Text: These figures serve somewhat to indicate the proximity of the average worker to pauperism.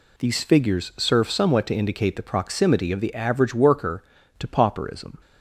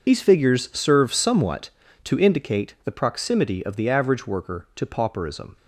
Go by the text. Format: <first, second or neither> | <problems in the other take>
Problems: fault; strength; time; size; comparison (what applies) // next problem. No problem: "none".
first | loses the start of "These"; at 0.0 s; 50 ms